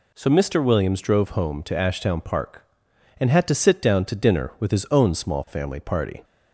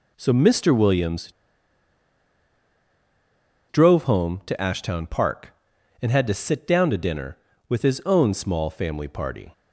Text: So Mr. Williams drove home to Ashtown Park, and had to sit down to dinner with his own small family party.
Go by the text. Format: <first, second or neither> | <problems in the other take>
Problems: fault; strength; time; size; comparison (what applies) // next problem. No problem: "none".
first | pauses between "Williams" and "drove"; strong; at 1.3 s; 2.3 s long